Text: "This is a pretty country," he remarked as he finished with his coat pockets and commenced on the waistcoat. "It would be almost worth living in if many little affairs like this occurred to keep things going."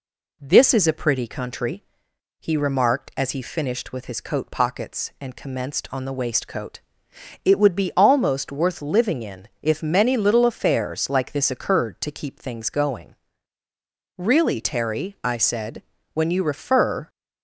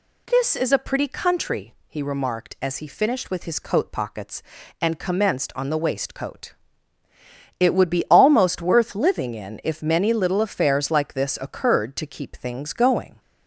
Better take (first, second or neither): second